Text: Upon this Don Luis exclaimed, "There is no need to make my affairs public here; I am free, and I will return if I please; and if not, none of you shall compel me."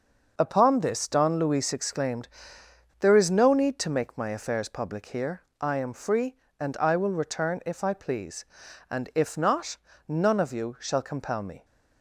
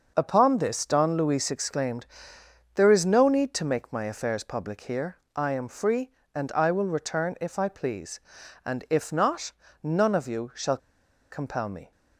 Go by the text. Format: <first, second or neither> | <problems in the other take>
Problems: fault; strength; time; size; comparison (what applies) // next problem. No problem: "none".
first | pauses between "shall" and "compel"; noticeable; at 10.7 s; 0.53 s long